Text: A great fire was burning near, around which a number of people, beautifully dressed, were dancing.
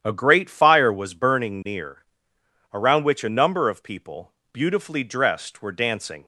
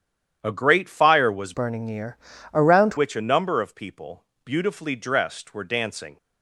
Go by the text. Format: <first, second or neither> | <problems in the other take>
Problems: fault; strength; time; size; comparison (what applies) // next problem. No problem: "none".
first | starts louder than the rest; strong; until 1.4 s; 9.5 dB; strong in the first // changes voice from "burning" to "around"; from 1.5 to 2.9 s; 1.4 s long